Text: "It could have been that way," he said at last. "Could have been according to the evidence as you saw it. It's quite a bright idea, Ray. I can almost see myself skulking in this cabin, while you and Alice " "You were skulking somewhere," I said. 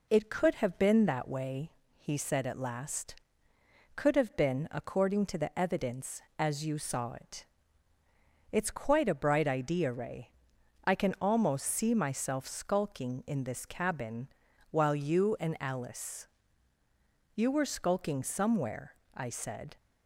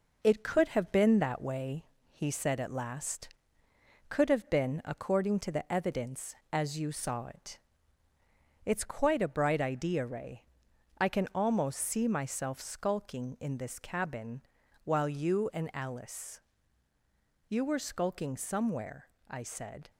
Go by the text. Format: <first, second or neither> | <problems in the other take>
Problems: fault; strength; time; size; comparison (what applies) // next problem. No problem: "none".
first | gets quieter; strong; throughout; 8.5 dB